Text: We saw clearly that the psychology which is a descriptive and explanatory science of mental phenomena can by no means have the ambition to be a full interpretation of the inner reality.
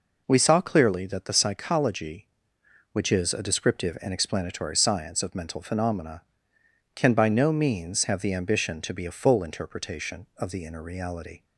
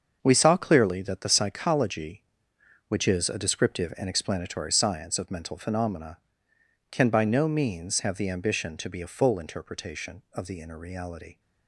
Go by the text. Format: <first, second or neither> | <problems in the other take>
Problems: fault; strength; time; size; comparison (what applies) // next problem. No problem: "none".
first | gets quieter; strong; throughout; 9.5 dB